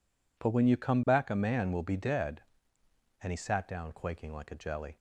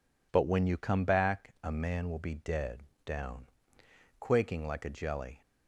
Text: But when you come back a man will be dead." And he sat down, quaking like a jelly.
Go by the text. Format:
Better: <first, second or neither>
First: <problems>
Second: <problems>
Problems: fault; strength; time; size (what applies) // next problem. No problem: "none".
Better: first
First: none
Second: skips "And he sat"; at 2.9 s